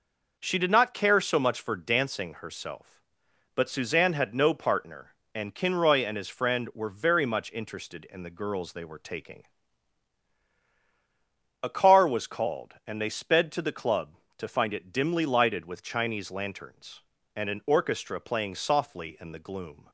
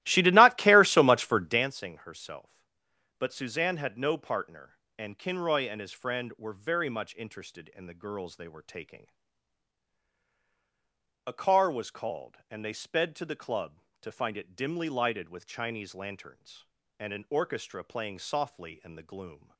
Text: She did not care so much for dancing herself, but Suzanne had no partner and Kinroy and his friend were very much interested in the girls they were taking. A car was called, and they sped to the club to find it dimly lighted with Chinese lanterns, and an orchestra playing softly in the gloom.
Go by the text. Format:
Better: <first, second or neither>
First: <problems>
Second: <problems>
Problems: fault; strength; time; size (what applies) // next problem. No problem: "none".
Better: first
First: none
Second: starts louder than the rest; strong; until 1.7 s; 15.5 dB